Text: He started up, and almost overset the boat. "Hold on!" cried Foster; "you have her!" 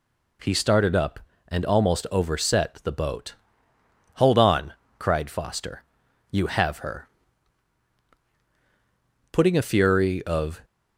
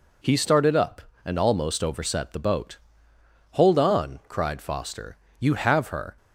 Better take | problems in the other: second | goes on to say "Putting a fury of"; noticeable; from 9.3 s on; 1.3 s long

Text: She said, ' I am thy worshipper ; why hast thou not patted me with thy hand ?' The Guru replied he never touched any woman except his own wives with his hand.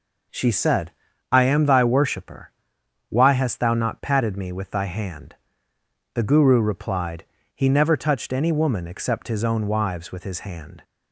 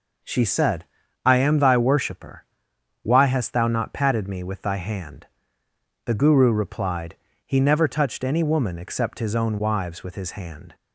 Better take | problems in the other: neither | pauses between "replied" and "he"; slight; the same in both

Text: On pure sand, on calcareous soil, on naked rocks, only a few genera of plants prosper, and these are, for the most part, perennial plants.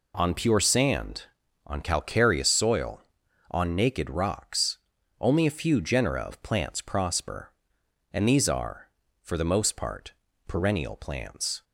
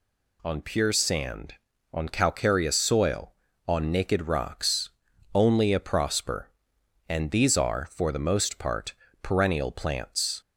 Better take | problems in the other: first | skips "few genera of plants"; at 5.7 s

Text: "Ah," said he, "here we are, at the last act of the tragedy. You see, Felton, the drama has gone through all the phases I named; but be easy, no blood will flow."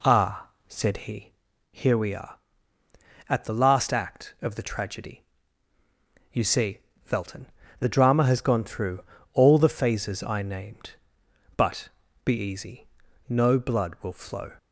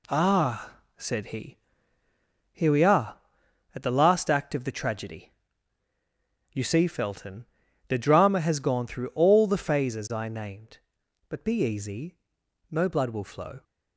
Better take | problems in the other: second | starts louder than the rest; slight; until 1.5 s; 2.5 dB // pauses between "through" and "all"; slight; at 9.0 s; 0.30 s long // pauses between "but" and "be"; slight; at 11.8 s; 0.36 s long

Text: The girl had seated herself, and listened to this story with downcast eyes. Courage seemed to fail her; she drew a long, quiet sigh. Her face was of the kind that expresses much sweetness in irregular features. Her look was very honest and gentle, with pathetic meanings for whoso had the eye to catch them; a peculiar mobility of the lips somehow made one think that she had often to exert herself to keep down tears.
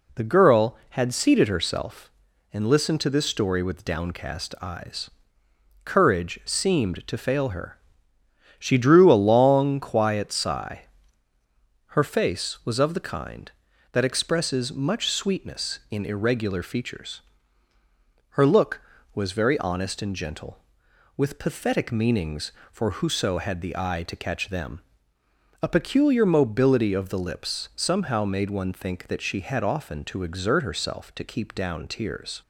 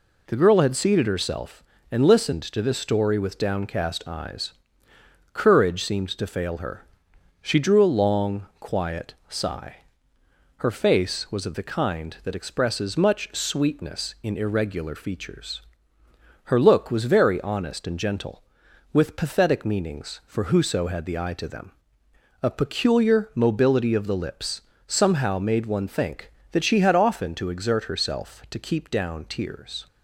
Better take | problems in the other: first | skips "catch"; at 21.4 s // pauses between "lips" and "somehow"; slight; at 24.6 s; 0.26 s long

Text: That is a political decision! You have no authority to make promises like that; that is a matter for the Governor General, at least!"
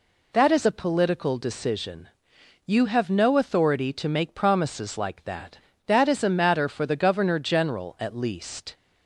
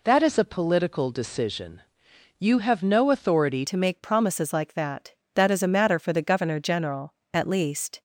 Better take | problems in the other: first | changes voice at "to"; from 3.6 s on; 4.4 s long

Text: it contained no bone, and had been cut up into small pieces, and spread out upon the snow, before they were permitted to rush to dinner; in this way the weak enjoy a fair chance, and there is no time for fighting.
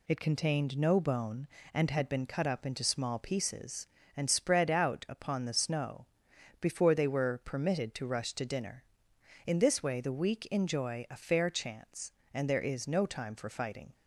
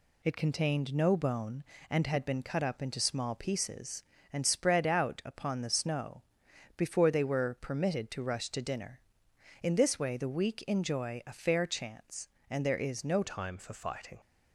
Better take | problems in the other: first | changes voice at "time"; from 13.2 s on; 0.9 s long

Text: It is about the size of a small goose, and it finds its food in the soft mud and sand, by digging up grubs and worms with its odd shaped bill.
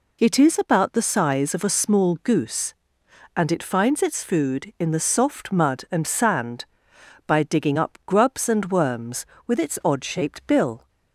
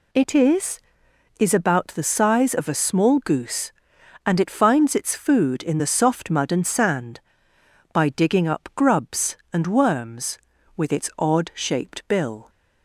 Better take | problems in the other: first | says "is" twice; at 1.3 s

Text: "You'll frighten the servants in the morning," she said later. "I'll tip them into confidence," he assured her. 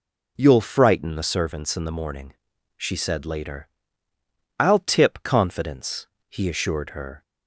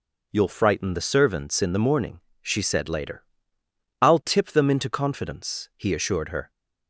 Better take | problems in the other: second | skips "them into"; at 5.2 s

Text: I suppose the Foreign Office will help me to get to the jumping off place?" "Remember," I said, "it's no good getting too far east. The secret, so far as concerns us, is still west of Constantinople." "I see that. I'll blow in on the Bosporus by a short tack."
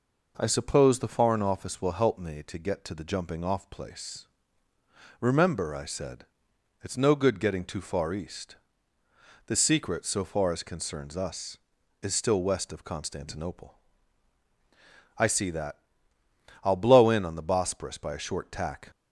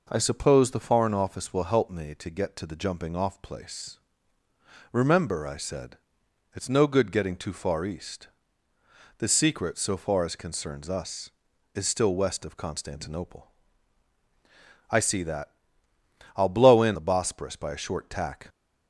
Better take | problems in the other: first | skips "on"; at 16.9 s

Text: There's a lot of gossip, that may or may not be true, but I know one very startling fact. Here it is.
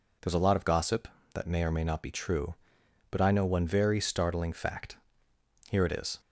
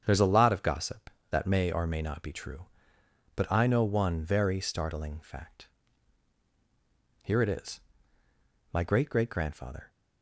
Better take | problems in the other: first | starts louder than the rest; strong; until 1.0 s; 7.5 dB // goes on to say "My great great grandfather"; noticeable; from 8.7 s on; 1.1 s long

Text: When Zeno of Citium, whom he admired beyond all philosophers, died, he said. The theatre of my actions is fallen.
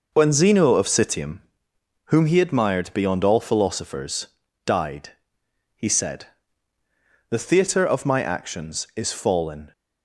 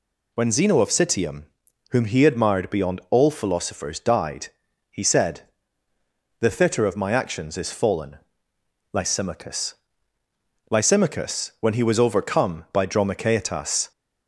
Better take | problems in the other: first | goes on to say "Lysimachus Lysimachus when he was overcome by Dromichaetas"; strong; from 8.9 s on; 4.9 s long

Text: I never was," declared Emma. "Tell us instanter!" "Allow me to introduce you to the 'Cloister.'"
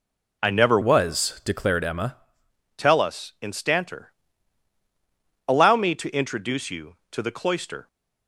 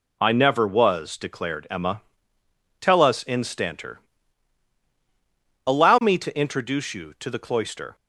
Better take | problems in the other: second | changes voice from "was" to "Emma"; from 0.8 to 2.1 s; 1.3 s long

